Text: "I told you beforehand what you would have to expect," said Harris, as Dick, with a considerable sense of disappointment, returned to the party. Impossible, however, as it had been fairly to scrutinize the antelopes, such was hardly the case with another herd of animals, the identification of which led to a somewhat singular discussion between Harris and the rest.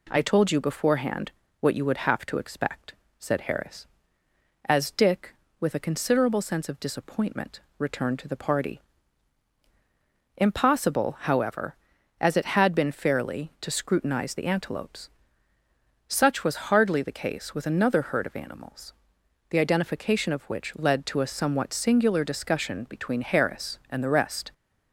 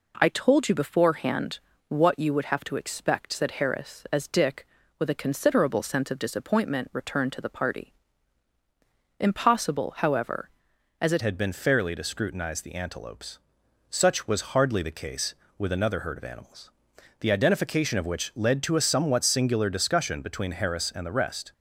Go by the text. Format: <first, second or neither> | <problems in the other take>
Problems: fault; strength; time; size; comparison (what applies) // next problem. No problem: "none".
first | pauses between "beforehand" and "what"; slight; at 1.5 s; 0.28 s long; slight in the first // changes voice at "had"; from 11.2 s on; 10.3 s long